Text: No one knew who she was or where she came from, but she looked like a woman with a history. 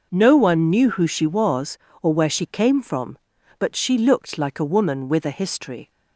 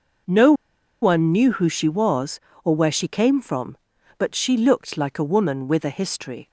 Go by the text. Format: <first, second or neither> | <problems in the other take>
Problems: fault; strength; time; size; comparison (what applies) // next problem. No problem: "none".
first | pauses between "No" and "one"; noticeable; at 0.5 s; 0.49 s long